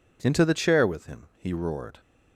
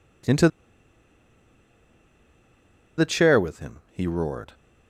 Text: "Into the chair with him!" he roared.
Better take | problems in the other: first | pauses between "Into" and "the"; strong; at 0.4 s; 2.4 s long

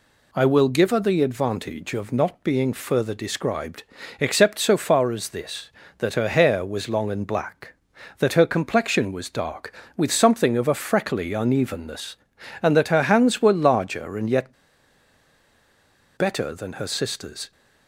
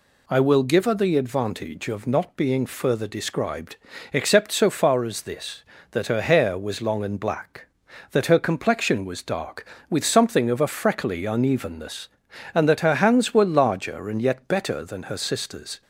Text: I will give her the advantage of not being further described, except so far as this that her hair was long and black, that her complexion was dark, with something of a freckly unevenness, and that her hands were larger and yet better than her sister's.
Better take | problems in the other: second | pauses between "yet" and "better"; strong; at 14.5 s; 1.6 s long

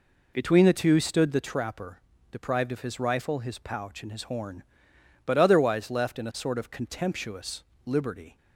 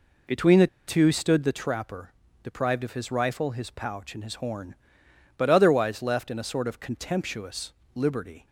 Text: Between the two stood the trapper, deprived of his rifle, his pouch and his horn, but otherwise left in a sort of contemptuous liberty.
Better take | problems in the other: first | pauses between "the" and "two"; slight; at 0.6 s; 0.21 s long // pauses between "contemptuous" and "liberty"; slight; at 7.7 s; 0.24 s long; slight in the first

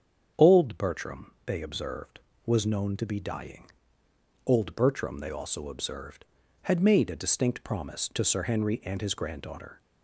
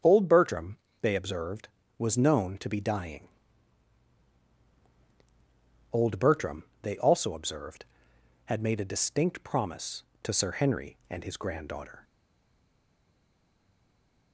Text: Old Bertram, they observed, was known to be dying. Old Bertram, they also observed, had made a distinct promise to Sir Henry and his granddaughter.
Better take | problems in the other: first | starts louder than the rest; until 1.2 s; 7 dB; strong in the first // stays silent after the last word; from 12.0 s on; 2.3 s long

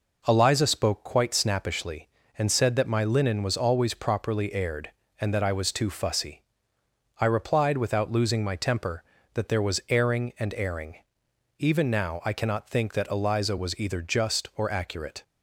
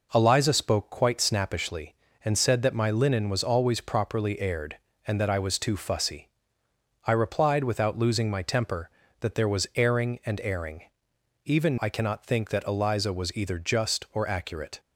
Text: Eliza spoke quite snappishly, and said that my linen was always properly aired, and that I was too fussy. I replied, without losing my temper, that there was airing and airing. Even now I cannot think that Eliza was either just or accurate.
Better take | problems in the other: first | skips "now"; at 11.7 s

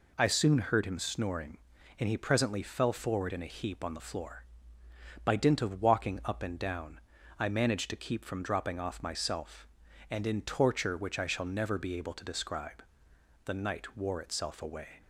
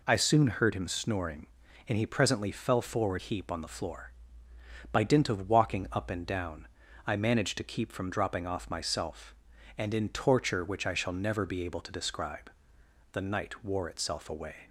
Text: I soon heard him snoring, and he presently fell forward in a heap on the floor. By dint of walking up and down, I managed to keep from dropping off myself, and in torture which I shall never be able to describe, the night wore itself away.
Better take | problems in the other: first | skips "in a"; at 3.2 s

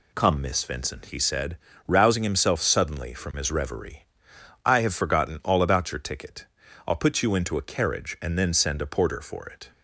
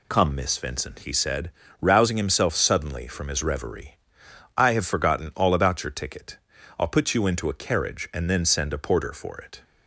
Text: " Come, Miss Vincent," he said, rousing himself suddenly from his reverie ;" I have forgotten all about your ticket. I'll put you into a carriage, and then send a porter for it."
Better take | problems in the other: neither | none

